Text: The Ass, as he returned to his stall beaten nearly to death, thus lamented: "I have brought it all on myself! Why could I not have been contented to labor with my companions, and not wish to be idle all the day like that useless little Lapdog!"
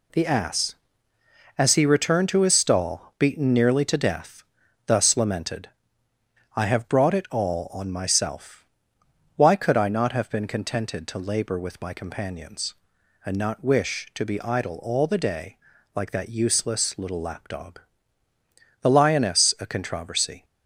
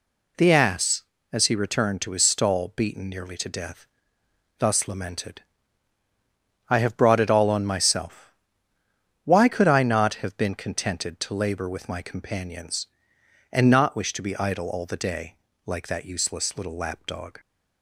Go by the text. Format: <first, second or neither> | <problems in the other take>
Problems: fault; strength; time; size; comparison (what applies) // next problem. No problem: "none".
second | pauses between "day" and "like"; slight; at 15.5 s; 0.36 s long; slight in the second // goes on to say "The Lioness A CONTROVERSY"; from 18.8 s on; 1.6 s long